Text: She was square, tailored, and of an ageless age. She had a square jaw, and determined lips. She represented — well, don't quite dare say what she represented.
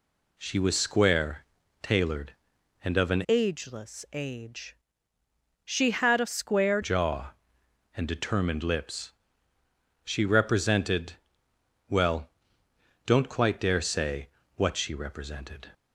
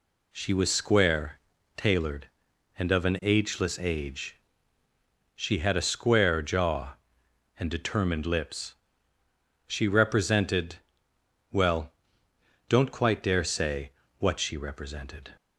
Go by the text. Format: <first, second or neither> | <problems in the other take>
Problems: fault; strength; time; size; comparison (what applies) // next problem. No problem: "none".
second | changes voice from "ageless" to "square"; from 3.2 to 6.7 s; 3.5 s long // pauses between "say" and "what"; slight; at 14.2 s; 0.26 s long; slight in the second